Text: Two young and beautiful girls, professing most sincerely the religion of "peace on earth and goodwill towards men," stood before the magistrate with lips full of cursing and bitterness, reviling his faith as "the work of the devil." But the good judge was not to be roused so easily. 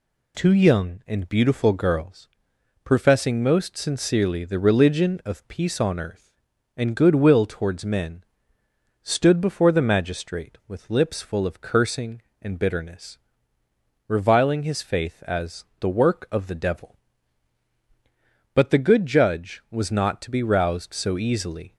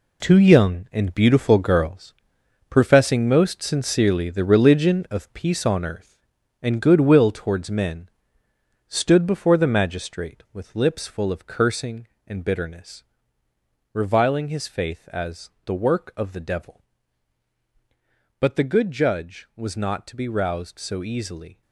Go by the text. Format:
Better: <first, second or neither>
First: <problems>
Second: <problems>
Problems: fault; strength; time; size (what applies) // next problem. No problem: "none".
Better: first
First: pauses between "as" and "the"; slight; at 15.6 s; 0.16 s long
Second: gets quieter; strong; throughout; 10 dB // pauses between "as" and "the"; slight; at 15.4 s; 0.16 s long